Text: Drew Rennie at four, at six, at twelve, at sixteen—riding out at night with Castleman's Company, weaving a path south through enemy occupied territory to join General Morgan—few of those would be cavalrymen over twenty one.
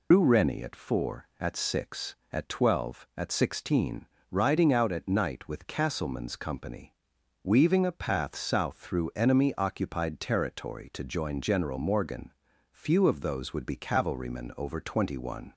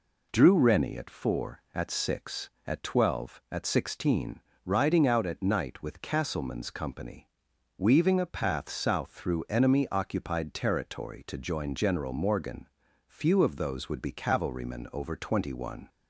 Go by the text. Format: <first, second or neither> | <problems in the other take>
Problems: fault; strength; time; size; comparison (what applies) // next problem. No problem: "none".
second | loses the start of "Drew"; at 0.1 s; 140 ms